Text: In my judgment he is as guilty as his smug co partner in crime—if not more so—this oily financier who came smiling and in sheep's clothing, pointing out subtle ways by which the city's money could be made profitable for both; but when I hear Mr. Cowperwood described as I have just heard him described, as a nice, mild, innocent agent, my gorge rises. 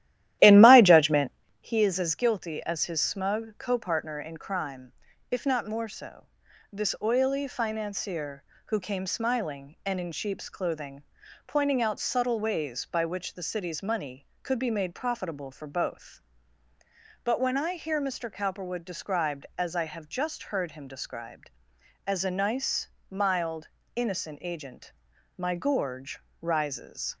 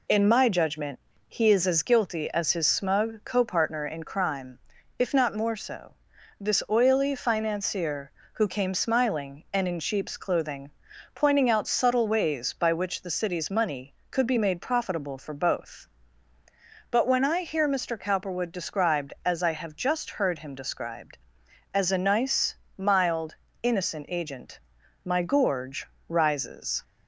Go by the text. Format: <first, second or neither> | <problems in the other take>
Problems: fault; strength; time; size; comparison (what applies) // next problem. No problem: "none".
second | starts louder than the rest; strong; until 1.4 s; 13.5 dB // pauses between "judgment" and "he"; slight; at 1.3 s; 0.28 s long; slight in the second // pauses between "gorge" and "rises"; slight; at 26.1 s; 0.22 s long; slight in the second